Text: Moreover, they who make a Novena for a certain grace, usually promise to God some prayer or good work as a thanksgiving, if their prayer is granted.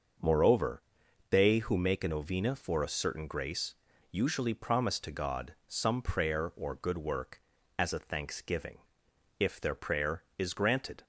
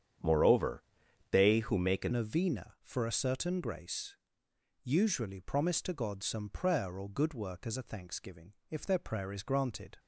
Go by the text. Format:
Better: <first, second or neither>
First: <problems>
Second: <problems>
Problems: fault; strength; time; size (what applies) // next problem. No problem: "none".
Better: first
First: starts louder than the rest; until 1.6 s; 6 dB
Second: starts louder than the rest; strong; until 1.7 s; 8.5 dB // changes voice at "Novena"; from 2.1 s on; 7.8 s long